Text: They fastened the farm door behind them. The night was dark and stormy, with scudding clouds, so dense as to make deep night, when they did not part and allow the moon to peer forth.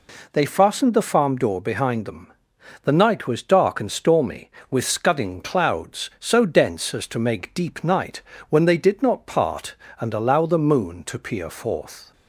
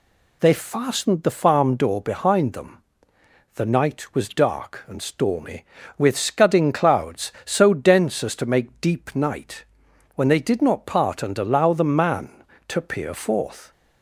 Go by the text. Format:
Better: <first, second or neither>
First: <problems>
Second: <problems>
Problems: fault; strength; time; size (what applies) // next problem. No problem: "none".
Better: first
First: none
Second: says "man" for "moon"; at 11.8 s